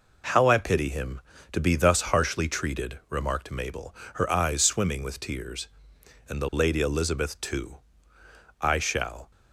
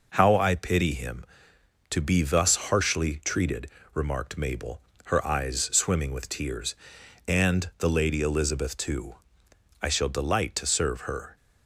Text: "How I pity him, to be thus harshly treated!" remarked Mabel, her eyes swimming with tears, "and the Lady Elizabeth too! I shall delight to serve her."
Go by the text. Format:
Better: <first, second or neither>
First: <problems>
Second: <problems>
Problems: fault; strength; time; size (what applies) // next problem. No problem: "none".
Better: second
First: stops before "delight to serve her"; at 9.3 s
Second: none